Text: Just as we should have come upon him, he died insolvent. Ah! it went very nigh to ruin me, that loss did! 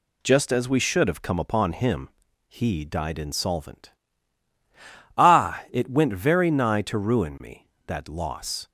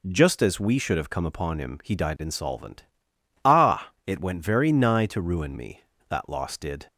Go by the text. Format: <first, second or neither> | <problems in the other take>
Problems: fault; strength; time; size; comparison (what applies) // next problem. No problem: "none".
second | stops before "did"; at 8.6 s